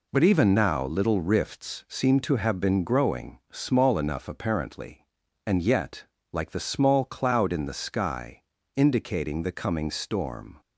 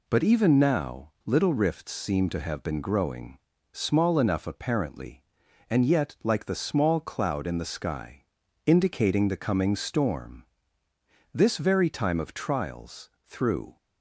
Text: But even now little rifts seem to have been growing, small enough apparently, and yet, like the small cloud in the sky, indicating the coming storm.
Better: first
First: none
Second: goes on to say "This very time of trials through"; strong; from 11.3 s on; 2.4 s long

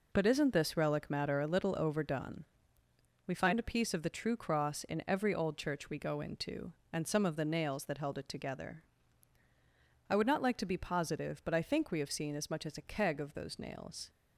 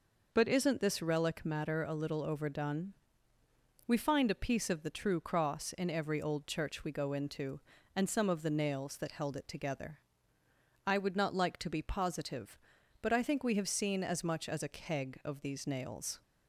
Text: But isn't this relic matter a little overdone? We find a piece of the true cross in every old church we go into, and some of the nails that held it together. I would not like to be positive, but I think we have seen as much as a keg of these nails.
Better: second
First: says "those" for "these"; at 13.3 s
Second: none

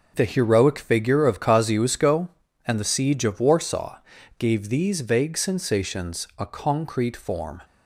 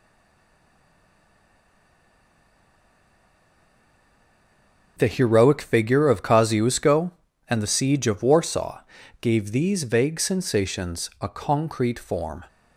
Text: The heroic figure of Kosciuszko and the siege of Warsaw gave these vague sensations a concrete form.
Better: first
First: pauses between "Warsaw" and "gave"; at 3.9 s; 0.40 s long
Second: stays silent before the first word; strong; until 4.9 s; 4.9 s long // pauses between "Warsaw" and "gave"; at 8.8 s; 0.40 s long

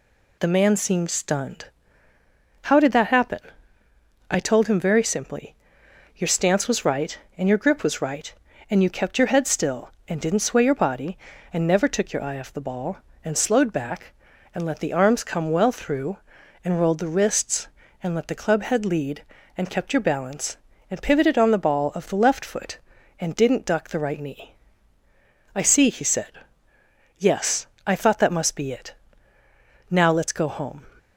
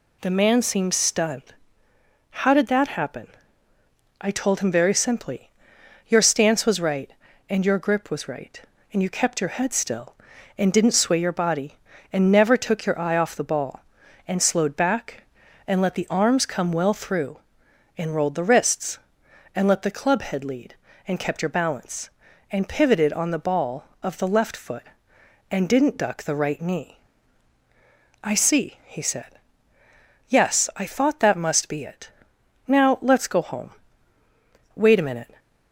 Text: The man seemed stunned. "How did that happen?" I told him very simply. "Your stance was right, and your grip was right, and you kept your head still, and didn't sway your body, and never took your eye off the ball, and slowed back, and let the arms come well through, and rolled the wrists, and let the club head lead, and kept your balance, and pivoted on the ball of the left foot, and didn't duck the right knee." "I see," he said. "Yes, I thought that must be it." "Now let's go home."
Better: first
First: none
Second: goes on to say "Wait a minute"; noticeable; from 34.7 s on; 0.64 s long

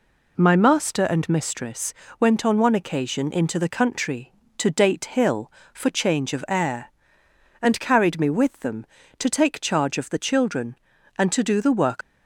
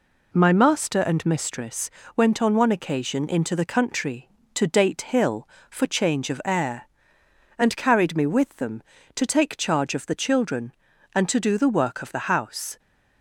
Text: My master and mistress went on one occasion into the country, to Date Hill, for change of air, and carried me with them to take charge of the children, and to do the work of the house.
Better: second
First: pauses between "mistress" and "went"; slight; at 1.9 s; 0.26 s long // stops before "of the house"; at 12.0 s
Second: pauses between "mistress" and "went"; slight; at 1.9 s; 0.26 s long

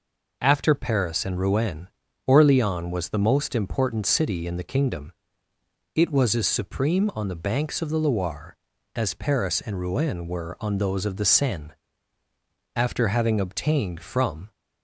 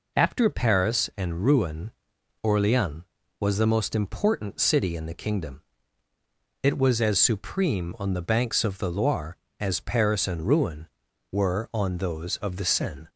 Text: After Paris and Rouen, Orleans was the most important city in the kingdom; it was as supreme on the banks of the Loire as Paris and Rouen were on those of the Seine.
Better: second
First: goes on to say "After having obtained from"; strong; from 12.7 s on; 1.7 s long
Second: none

